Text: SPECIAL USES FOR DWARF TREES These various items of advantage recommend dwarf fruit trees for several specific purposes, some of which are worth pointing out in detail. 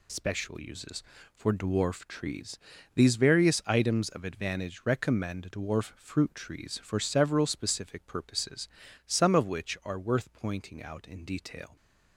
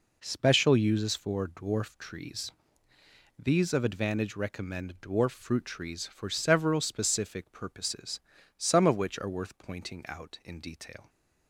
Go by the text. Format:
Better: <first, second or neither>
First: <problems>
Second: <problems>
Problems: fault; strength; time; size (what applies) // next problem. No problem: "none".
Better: first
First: pauses between "TREES" and "These"; slight; at 2.5 s; 0.36 s long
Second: pauses between "TREES" and "These"; noticeable; at 2.5 s; 0.90 s long // skips "various items"; at 3.7 s